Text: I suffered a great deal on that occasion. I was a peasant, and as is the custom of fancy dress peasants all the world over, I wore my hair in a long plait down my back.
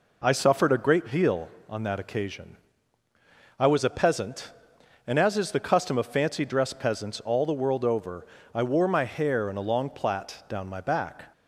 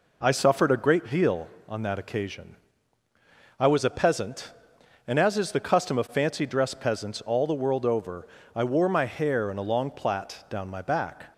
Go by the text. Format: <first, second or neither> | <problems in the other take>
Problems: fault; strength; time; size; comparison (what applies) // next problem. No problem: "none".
neither | none